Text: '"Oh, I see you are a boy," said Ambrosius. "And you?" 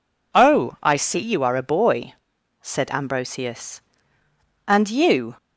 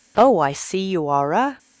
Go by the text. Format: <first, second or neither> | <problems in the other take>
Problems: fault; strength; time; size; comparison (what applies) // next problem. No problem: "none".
first | stops before "boy said Ambrosius And you"; at 1.5 s